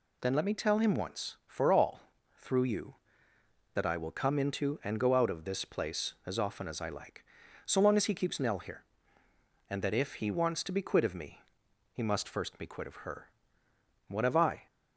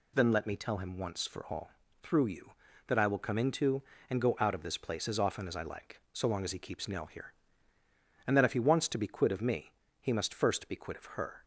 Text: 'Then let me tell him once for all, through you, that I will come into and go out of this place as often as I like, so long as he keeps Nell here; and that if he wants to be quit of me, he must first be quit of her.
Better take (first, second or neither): second